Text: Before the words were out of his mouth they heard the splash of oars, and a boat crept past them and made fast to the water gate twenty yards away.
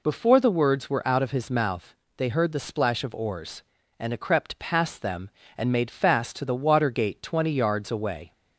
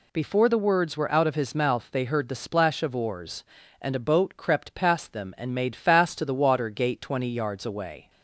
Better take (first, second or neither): second